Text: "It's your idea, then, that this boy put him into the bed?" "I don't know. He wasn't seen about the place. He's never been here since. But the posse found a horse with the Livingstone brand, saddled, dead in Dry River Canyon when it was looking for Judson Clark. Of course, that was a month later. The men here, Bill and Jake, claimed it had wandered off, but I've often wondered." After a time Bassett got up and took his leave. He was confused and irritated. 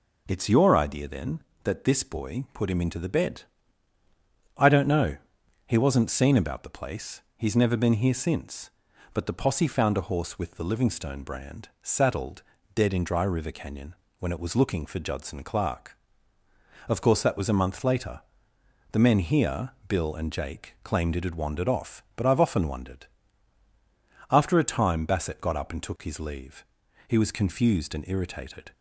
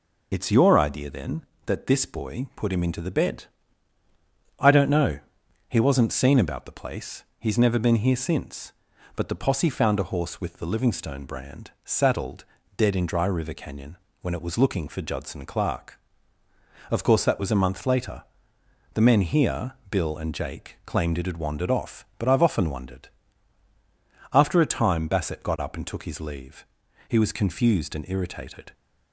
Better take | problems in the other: first | loses the start of "It's"; at 0.3 s; 35 ms // pauses between "Canyon" and "when"; slight; at 13.9 s; 0.24 s long; slight in the first

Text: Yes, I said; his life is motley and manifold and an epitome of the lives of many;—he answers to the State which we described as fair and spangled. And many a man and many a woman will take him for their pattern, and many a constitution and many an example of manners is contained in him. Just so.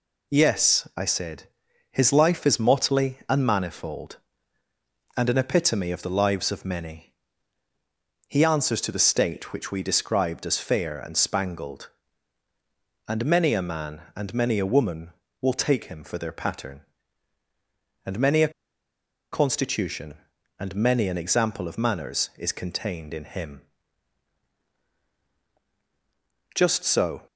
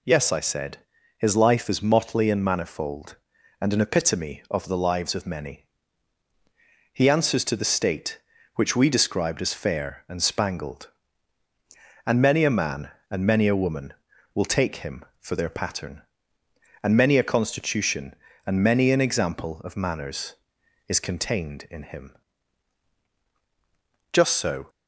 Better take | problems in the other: second | pauses between "a" and "constitution"; noticeable; at 18.5 s; 0.82 s long

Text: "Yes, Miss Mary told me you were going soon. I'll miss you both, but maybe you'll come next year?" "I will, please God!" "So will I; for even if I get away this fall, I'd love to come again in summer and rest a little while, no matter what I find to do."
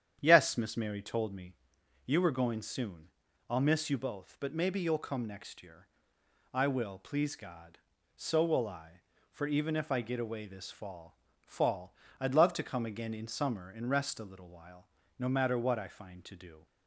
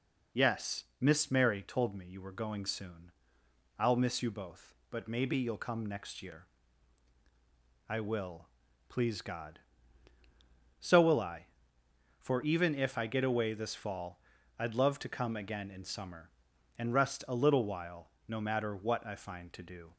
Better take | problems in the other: second | starts louder than the rest; strong; until 1.2 s; 9 dB // pauses between "me" and "you"; noticeable; at 1.5 s; 0.51 s long // says "fall" twice; at 11.4 s

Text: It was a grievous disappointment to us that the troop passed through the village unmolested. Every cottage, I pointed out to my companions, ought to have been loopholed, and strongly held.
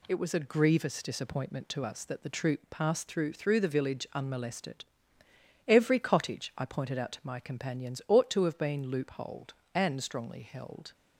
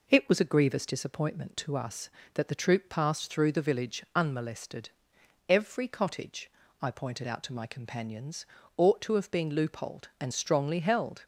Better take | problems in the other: second | says "through" twice; at 3.3 s

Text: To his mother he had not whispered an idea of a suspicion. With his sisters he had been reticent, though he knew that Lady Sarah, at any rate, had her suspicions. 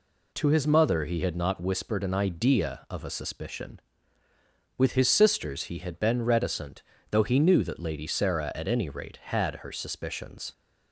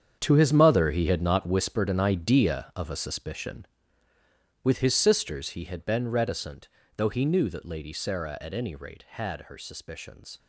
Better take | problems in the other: first | gets quieter; strong; throughout; 12.5 dB

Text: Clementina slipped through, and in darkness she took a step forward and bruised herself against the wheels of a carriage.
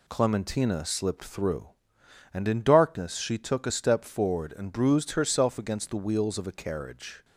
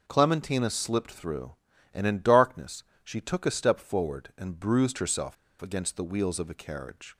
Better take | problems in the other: first | pauses between "darkness" and "she"; slight; at 2.8 s; 0.20 s long // pauses between "herself" and "against"; slight; at 5.3 s; 0.27 s long

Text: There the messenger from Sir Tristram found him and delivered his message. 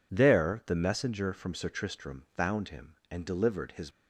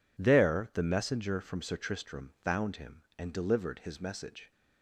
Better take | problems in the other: second | stops before "message"; at 3.9 s

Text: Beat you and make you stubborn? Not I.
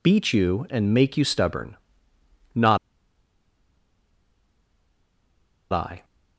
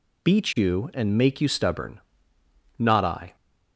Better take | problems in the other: second | pauses between "Not" and "I"; strong; at 2.7 s; 2.9 s long

